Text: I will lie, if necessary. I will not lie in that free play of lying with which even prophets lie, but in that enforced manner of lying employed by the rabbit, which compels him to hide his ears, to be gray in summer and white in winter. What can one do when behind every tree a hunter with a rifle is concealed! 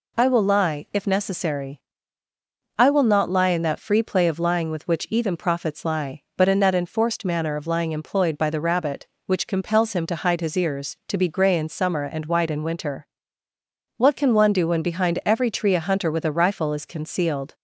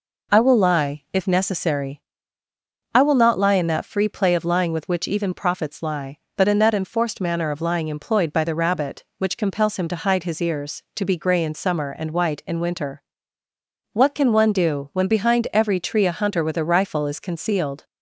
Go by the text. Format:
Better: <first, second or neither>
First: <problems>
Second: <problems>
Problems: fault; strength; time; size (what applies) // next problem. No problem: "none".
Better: neither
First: none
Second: none